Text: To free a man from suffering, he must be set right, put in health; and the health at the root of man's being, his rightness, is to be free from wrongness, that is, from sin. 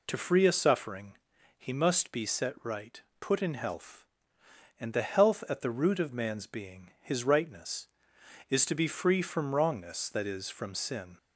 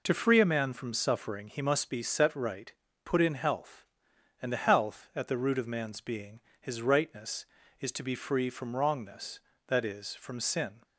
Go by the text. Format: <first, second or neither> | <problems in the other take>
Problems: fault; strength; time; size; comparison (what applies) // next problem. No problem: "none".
second | skips "man from"; at 0.5 s